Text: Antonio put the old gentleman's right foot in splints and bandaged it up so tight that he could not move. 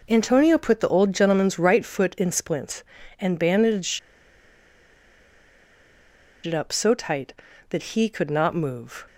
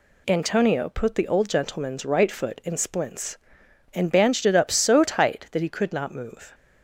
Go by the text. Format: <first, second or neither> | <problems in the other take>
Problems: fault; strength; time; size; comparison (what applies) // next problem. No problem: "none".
second | pauses between "bandaged" and "it"; strong; at 3.9 s; 2.4 s long